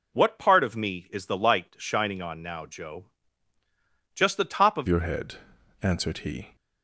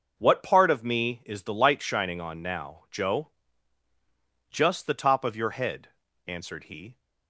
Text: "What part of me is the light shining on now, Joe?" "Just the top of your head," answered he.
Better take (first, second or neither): second